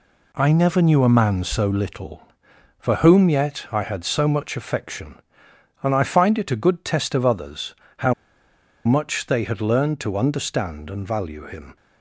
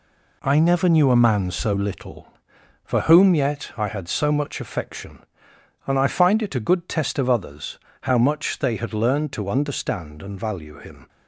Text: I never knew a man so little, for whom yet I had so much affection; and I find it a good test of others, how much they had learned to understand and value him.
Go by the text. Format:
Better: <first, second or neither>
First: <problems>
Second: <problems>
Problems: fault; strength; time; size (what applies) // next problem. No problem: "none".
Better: second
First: pauses between "how" and "much"; noticeable; at 8.1 s; 0.71 s long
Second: none